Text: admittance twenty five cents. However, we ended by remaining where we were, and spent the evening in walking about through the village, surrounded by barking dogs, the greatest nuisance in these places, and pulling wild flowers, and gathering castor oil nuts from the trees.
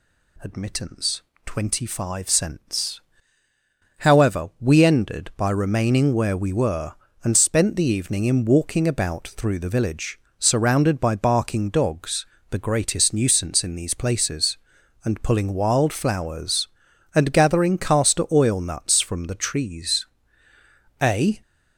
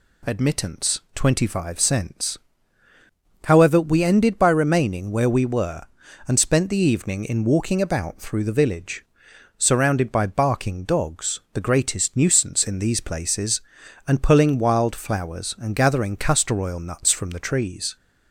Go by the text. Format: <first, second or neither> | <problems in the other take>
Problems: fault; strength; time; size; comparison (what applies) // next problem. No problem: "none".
second | pauses between "admittance" and "twenty"; slight; at 1.2 s; 0.24 s long // goes on to say "A"; slight; from 21.0 s on; 0.40 s long